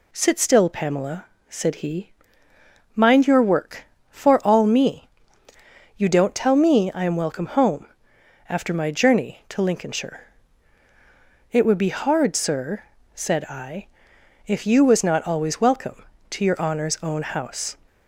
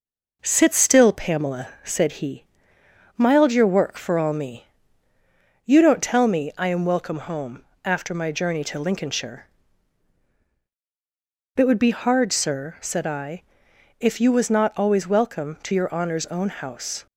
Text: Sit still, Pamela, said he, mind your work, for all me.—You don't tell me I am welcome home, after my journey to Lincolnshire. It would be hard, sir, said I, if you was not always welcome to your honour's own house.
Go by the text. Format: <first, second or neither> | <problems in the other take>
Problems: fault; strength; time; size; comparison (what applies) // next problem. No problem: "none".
first | says "mild" for "mind"; at 3.1 s